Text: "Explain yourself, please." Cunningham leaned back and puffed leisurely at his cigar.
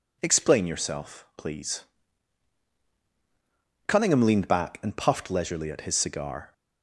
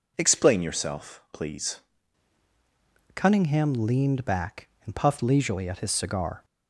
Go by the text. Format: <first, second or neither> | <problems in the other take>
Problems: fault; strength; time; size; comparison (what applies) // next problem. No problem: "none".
first | changes voice at "Cunningham"; from 3.1 s on; 3.3 s long